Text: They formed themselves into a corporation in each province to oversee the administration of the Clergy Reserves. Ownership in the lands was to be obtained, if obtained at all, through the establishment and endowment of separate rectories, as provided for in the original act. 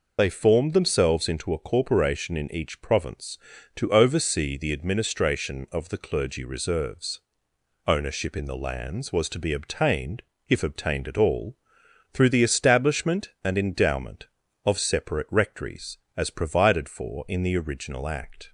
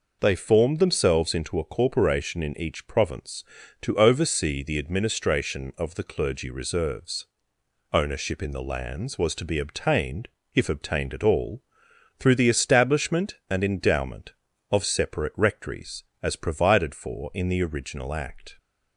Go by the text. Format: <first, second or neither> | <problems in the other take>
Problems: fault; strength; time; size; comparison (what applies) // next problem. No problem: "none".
second | loses the start of "They"; at 0.1 s; 35 ms